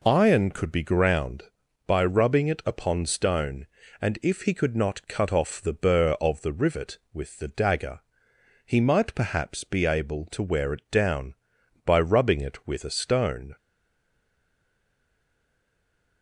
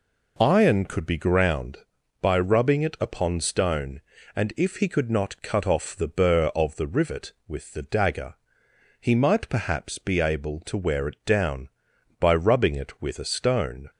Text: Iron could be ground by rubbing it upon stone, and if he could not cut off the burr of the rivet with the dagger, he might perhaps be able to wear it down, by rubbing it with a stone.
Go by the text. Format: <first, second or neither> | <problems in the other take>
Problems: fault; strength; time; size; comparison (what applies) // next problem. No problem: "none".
second | stays silent after the last word; strong; from 13.5 s on; 2.7 s long